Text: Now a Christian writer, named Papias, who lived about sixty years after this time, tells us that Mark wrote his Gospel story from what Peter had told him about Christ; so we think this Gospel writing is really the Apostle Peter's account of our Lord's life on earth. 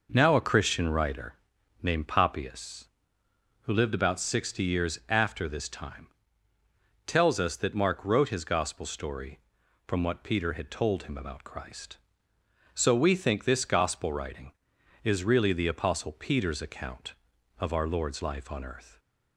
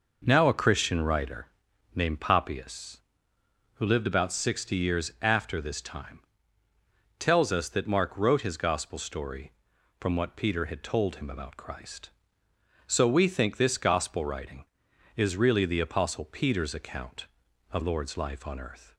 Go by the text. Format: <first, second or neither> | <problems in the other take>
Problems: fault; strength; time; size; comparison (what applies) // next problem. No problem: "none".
first | skips "our"; at 17.8 s